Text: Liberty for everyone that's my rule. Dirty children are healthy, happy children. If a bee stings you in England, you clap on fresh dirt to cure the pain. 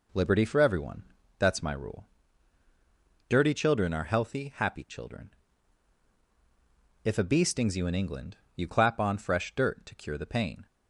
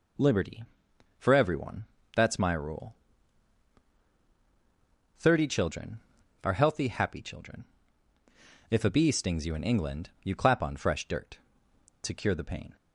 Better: first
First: pauses between "everyone" and "that's"; slight; at 1.0 s; 0.34 s long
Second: pauses between "everyone" and "that's"; slight; at 1.8 s; 0.30 s long // says "Thirty" for "Dirty"; at 5.1 s

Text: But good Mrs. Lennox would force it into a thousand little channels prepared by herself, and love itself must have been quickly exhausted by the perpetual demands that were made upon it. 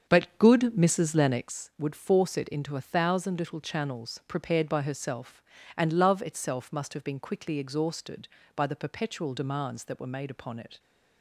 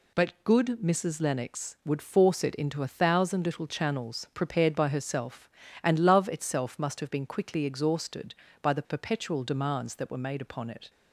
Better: second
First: starts louder than the rest; strong; until 1.5 s; 7 dB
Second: none

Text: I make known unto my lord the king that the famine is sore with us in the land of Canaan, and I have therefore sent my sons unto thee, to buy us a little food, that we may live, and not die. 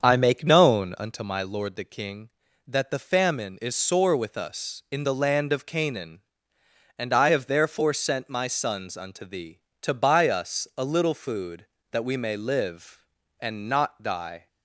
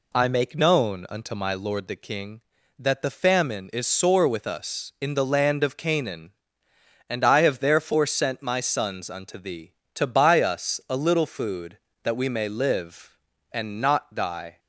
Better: second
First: starts louder than the rest; until 1.2 s; 7 dB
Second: none

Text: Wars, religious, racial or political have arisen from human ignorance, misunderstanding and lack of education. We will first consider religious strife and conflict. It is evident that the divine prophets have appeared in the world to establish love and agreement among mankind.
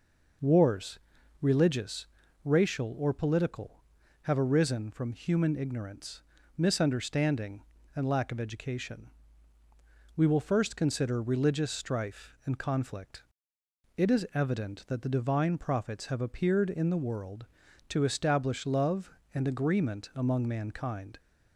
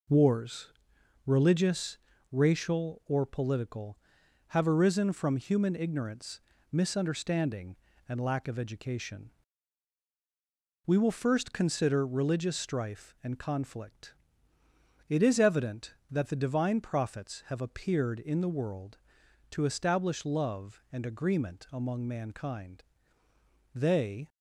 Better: first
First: none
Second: goes on to say "They"; from 23.7 s on; 0.54 s long

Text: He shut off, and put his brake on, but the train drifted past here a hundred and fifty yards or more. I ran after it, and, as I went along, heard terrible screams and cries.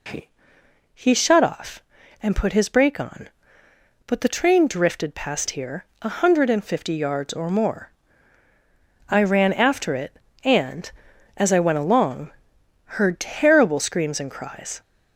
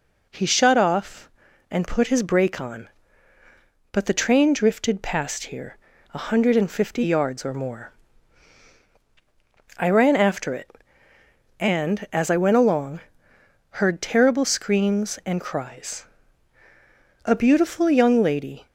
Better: first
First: pauses between "here" and "a"; slight; at 5.8 s; 0.18 s long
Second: pauses between "here" and "a"; slight; at 5.7 s; 0.34 s long // goes on to say "A beautiful young lady"; from 17.2 s on; 1.4 s long

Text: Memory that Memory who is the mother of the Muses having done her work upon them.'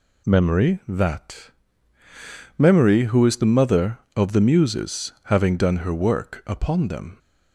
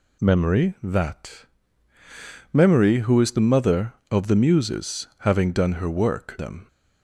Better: first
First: pauses between "that" and "Memory"; at 1.4 s; 1.0 s long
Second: pauses between "that" and "Memory"; at 1.4 s; 1.0 s long // skips "upon"; at 6.3 s

